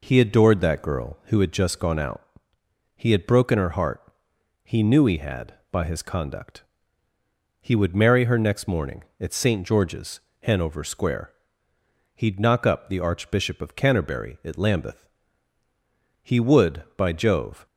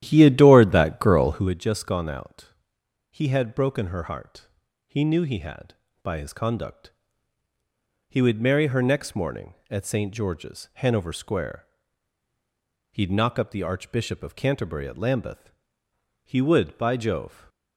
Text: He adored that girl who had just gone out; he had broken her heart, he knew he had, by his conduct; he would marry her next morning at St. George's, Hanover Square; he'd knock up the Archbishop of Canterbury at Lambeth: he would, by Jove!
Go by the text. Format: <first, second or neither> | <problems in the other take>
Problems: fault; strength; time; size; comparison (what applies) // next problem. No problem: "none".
first | starts louder than the rest; strong; until 1.5 s; 12 dB